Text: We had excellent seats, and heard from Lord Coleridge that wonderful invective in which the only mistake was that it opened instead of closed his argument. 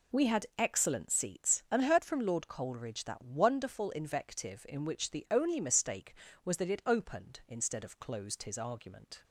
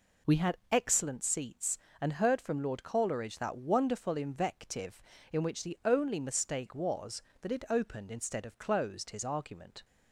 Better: neither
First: none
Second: none

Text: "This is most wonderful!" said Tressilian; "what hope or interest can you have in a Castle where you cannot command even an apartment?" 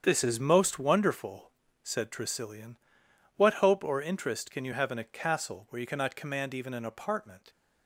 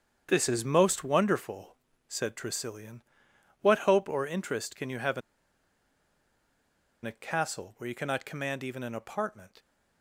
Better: first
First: starts louder than the rest; strong; until 1.0 s; 8 dB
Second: starts louder than the rest; strong; until 1.3 s; 8 dB // pauses between "in" and "a"; strong; at 5.2 s; 1.8 s long

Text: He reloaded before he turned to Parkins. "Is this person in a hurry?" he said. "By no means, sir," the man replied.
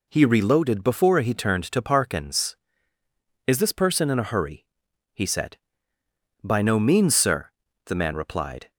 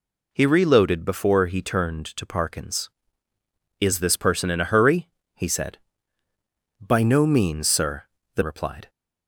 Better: first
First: none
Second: skips "man"; at 8.4 s

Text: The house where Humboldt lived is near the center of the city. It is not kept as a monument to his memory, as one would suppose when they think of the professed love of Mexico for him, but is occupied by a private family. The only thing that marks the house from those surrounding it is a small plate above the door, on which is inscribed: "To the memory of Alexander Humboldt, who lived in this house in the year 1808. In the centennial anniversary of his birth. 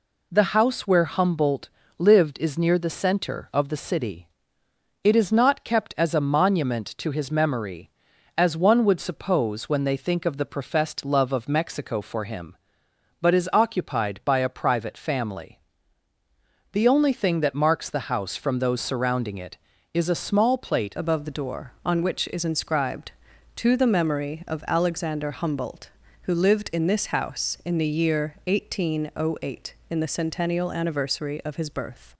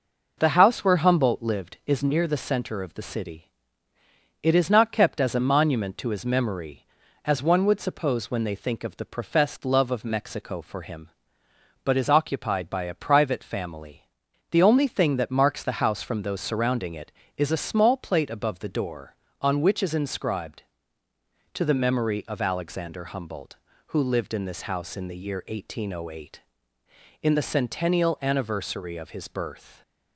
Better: second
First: pauses between "Humboldt" and "lived"; slight; at 1.6 s; 0.28 s long // changes voice at "above"; from 20.9 s on; 11.2 s long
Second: none

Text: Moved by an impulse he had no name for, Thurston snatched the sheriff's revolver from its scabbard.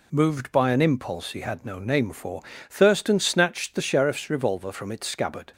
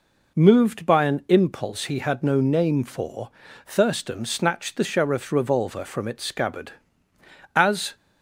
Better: first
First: none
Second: goes on to say "As"; slight; from 7.5 s on; 0.40 s long

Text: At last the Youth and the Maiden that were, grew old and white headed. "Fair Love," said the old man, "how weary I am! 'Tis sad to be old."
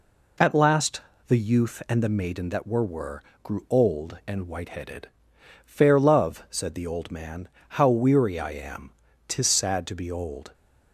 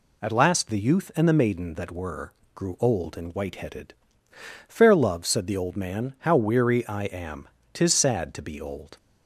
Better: second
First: pauses between "last" and "the"; slight; at 1.0 s; 0.26 s long // says "were" twice; at 2.8 s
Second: none

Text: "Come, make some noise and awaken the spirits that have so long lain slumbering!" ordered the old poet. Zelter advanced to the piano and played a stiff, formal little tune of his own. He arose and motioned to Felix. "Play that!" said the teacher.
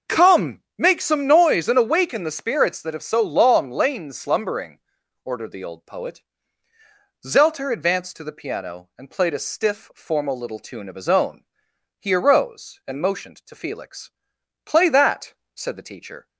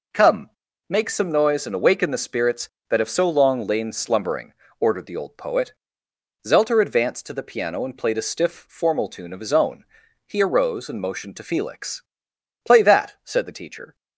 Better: first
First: none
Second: skips "little"; at 9.0 s

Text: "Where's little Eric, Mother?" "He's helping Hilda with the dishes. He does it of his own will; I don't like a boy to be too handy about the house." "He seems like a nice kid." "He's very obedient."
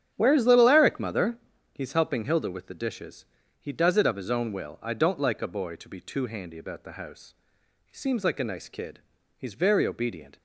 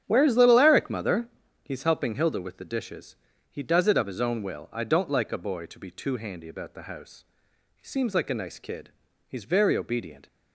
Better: neither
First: starts louder than the rest; strong; until 1.1 s; 9 dB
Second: starts louder than the rest; strong; until 1.0 s; 9 dB

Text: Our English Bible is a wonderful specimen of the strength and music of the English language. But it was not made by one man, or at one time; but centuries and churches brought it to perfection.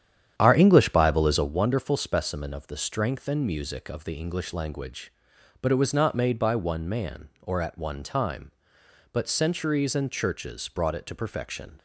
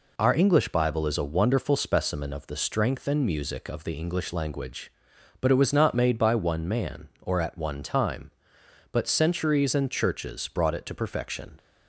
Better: second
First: starts louder than the rest; strong; until 1.6 s; 9.5 dB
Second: none

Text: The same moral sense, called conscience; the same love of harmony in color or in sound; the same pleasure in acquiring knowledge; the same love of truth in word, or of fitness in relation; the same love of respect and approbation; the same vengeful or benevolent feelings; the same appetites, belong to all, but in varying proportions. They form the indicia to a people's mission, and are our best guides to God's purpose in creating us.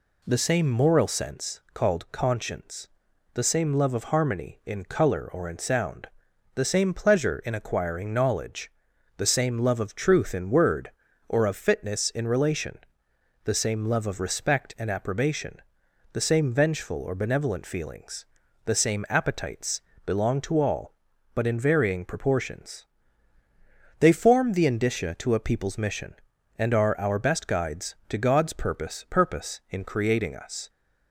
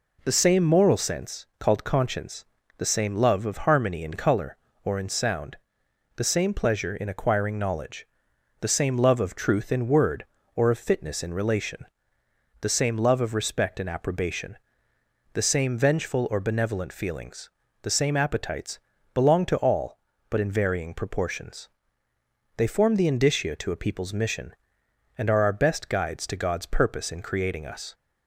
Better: second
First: says "purpose" twice; at 29.0 s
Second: none

